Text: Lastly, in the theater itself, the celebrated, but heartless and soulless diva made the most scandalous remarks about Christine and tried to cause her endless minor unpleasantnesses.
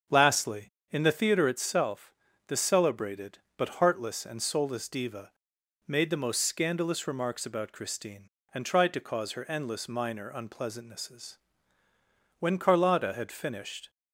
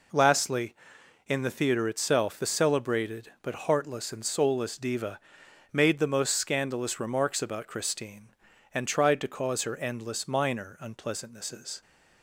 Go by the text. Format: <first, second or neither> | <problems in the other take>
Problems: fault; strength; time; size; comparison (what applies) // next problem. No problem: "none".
second | starts louder than the rest; until 1.3 s; 6.5 dB // pauses between "diva" and "made"; noticeable; at 5.3 s; 0.56 s long; noticeable in the second // goes on to say "When Carlotta had finished"; from 12.3 s on; 1.5 s long